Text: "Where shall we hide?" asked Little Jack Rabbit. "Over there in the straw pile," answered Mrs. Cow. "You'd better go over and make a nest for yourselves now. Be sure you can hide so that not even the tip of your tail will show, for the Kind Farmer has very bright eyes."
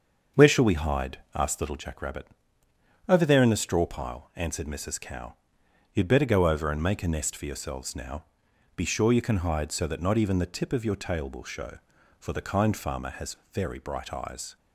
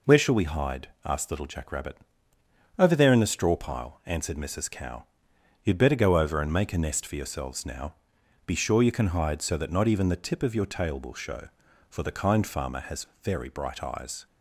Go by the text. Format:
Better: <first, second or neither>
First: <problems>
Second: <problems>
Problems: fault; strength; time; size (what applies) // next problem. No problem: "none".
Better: second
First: starts louder than the rest; until 2.0 s; 6.5 dB // pauses between "has" and "very"; slight; at 13.3 s; 0.16 s long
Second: pauses between "has" and "very"; slight; at 13.0 s; 0.16 s long